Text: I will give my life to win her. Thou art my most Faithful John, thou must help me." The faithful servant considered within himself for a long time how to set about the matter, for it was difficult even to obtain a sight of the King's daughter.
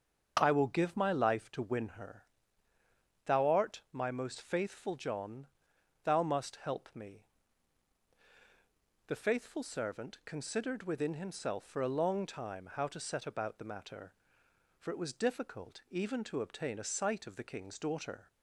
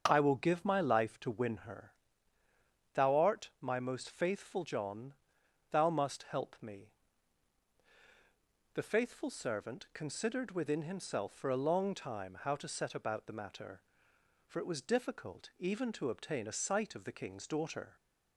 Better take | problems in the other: neither | starts louder than the rest; the same in both

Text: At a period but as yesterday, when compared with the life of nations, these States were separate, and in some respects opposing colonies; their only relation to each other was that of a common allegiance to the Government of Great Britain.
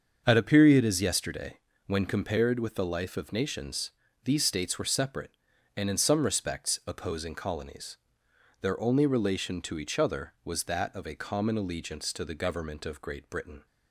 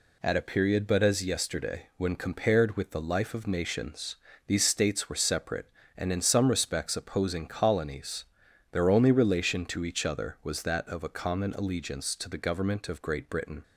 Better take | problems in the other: second | starts louder than the rest; until 1.2 s; 7 dB // skips "but"; at 0.8 s

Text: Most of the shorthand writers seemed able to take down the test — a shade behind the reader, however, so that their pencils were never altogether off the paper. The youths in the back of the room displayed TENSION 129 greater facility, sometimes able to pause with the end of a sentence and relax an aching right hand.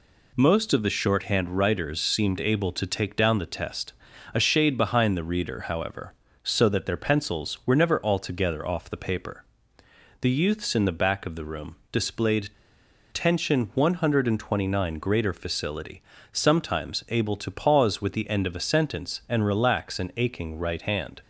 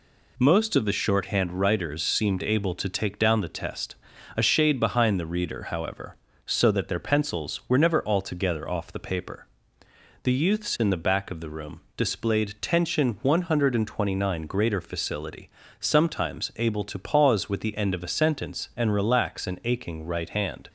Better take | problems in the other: second | pauses between "room" and "displayed"; slight; at 11.7 s; 0.16 s long; slight in the second // pauses between "displayed" and "TENSION"; noticeable; at 12.4 s; 0.63 s long

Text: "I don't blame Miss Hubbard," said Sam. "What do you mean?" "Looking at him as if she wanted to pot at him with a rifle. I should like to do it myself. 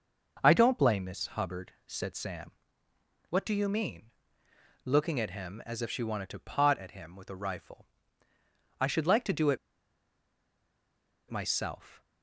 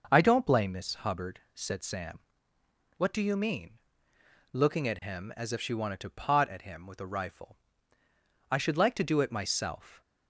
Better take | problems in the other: second | pauses between "it" and "myself"; strong; at 9.5 s; 1.7 s long

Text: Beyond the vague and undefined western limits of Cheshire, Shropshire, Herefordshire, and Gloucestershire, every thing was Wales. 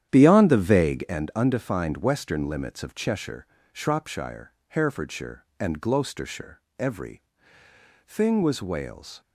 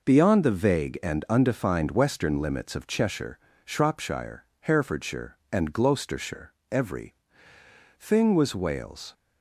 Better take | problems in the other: second | starts louder than the rest; strong; until 1.2 s; 10 dB // pauses between "every" and "thing"; noticeable; at 7.2 s; 0.86 s long; noticeable in the second

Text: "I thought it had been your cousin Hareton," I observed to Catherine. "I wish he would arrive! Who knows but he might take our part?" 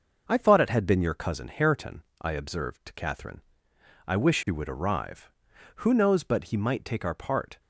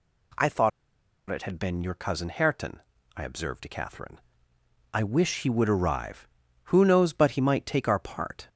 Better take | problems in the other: first | pauses between "thought" and "it"; noticeable; at 0.7 s; 0.60 s long

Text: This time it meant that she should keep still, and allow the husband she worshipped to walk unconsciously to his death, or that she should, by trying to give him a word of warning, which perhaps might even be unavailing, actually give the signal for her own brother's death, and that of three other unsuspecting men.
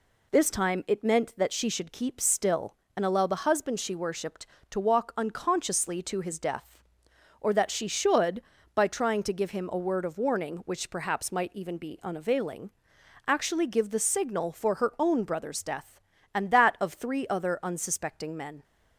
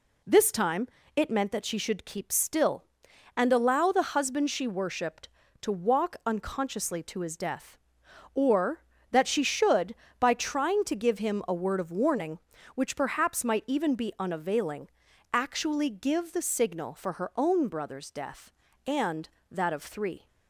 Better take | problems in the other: first | pauses between "time" and "it"; slight; at 0.8 s; 0.28 s long // stops before "other unsuspecting men"; at 20.2 s

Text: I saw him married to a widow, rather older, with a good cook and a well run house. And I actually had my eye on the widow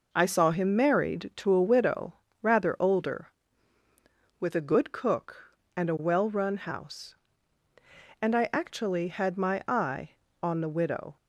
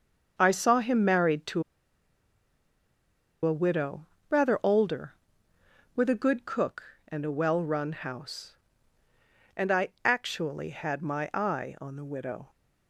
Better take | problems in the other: first | starts louder than the rest; until 1.4 s; 7 dB // pauses between "to" and "a"; strong; at 1.6 s; 1.8 s long // pauses between "I" and "actually"; slight; at 9.8 s; 0.16 s long

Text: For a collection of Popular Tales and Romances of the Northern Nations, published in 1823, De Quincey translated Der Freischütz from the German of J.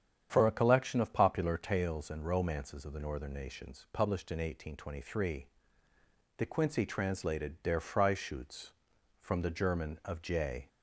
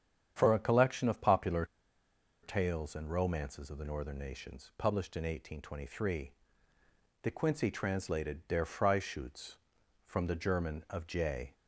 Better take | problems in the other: first | starts louder than the rest; strong; until 1.3 s; 8.5 dB; strong in the first // pauses between "Popular" and "Tales"; noticeable; at 1.6 s; 0.77 s long

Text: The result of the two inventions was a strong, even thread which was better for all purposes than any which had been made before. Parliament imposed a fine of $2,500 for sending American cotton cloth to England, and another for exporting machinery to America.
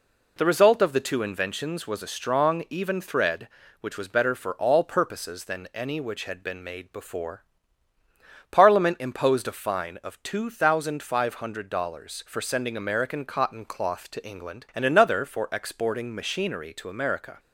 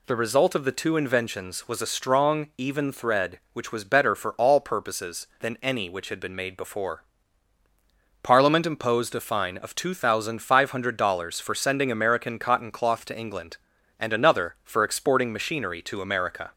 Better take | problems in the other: neither | none

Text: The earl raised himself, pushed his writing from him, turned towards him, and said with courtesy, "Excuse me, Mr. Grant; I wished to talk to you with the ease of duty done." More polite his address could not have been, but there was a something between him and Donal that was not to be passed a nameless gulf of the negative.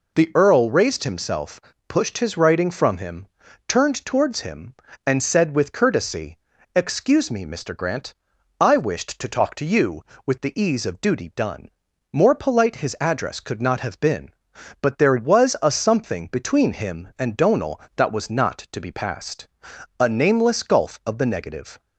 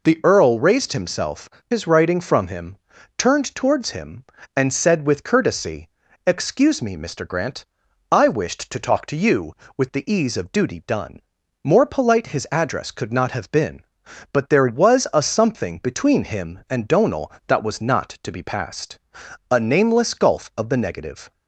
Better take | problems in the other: first | skips "pushed"; at 1.5 s // pauses between "passed" and "a"; noticeable; at 18.9 s; 0.50 s long; noticeable in the first

